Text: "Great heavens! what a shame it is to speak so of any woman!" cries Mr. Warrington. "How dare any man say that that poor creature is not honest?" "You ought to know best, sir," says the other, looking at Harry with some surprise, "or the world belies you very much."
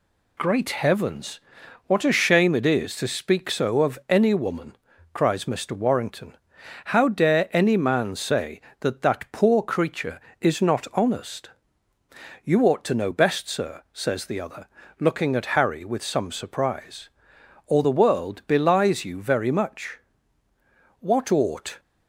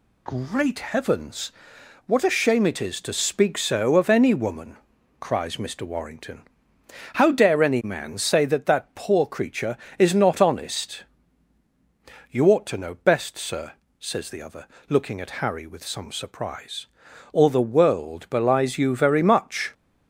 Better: second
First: goes on to say "What ought"; noticeable; from 20.9 s on; 0.80 s long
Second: none

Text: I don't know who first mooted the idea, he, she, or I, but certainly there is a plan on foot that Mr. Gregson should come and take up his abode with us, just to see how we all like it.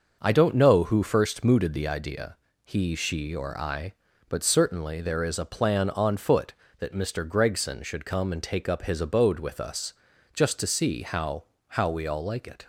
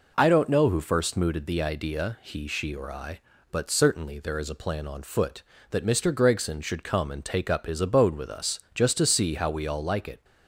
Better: second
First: starts louder than the rest; until 1.2 s; 6 dB // says "how" twice; at 11.6 s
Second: none

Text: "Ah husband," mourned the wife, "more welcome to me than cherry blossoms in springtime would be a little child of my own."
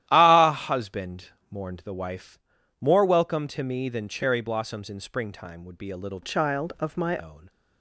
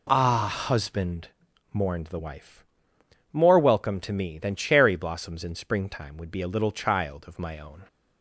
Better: second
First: starts louder than the rest; strong; until 1.0 s; 13 dB // changes voice from "child" to "my"; from 6.2 to 7.1 s; 0.9 s long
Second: none

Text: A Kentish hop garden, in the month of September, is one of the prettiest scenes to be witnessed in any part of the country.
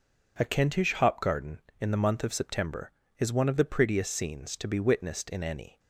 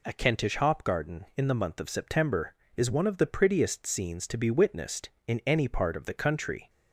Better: second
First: stops before "part of the country"; at 5.7 s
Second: none

